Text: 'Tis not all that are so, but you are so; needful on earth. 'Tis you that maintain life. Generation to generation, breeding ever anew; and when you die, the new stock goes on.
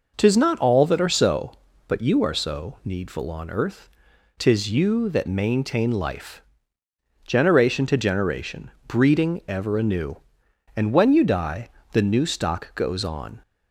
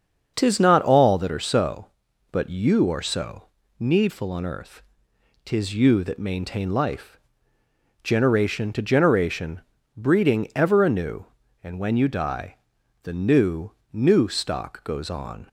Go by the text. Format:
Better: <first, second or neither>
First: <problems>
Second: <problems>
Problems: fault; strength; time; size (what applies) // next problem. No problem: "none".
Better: first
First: none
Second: starts louder than the rest; until 1.3 s; 6.5 dB // says "new" twice; at 13.9 s